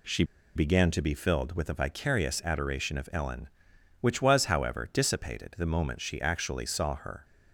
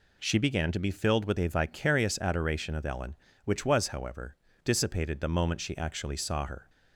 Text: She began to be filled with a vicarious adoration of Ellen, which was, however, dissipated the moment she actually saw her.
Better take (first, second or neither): second